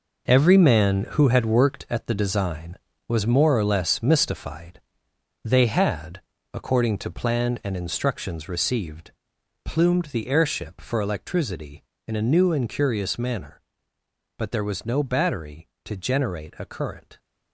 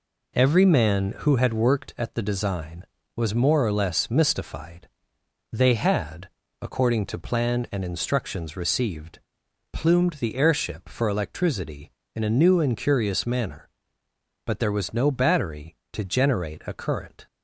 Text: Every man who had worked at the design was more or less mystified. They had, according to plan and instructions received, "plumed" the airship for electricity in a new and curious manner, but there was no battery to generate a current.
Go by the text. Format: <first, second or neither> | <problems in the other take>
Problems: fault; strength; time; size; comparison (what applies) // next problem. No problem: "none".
second | gets quieter; strong; throughout; 9.5 dB